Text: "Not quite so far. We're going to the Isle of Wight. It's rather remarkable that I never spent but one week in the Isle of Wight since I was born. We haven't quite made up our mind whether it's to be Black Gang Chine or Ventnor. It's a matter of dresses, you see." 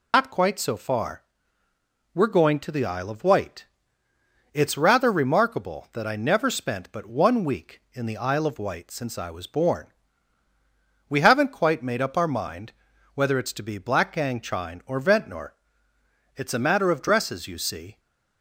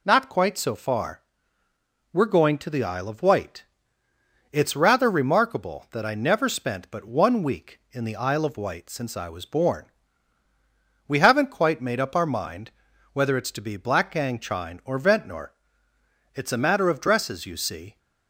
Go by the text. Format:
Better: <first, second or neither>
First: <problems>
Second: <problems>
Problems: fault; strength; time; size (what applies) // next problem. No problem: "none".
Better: second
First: loses the start of "Not"; at 0.1 s; 70 ms // pauses between "mind" and "whether"; at 12.7 s; 0.40 s long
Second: pauses between "mind" and "whether"; at 12.7 s; 0.40 s long